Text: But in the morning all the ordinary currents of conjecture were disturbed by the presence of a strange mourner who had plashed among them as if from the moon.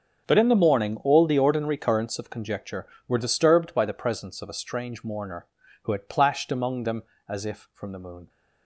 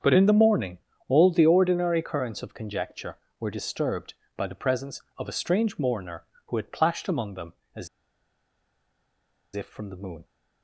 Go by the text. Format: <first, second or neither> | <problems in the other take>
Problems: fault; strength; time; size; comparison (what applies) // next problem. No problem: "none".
first | starts louder than the rest; strong; until 1.3 s; 7 dB; strong in the first // pauses between "morning" and "all"; slight; at 0.7 s; 0.30 s long // pauses between "as" and "if"; strong; at 7.8 s; 1.6 s long